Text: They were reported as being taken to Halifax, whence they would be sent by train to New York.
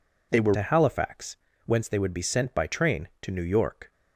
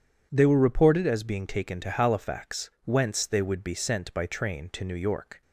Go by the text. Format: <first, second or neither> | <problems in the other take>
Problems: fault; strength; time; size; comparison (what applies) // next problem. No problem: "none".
second | skips "reported as being taken"; at 0.5 s